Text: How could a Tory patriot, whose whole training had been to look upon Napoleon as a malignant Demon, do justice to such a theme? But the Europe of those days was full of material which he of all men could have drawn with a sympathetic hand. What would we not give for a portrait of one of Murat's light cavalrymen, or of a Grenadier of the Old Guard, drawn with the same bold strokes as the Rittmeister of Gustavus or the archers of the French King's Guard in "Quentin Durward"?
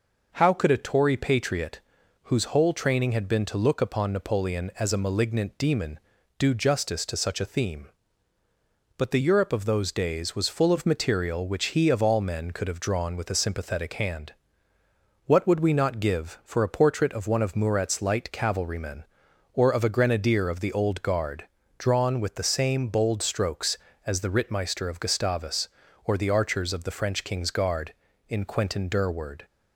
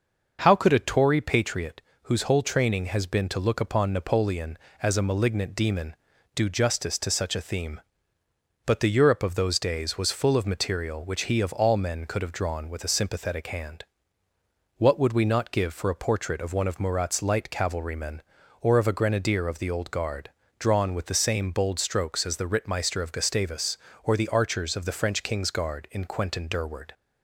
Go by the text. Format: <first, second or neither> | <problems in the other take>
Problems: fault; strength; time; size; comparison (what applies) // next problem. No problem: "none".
first | says "has" for "had"; at 2.8 s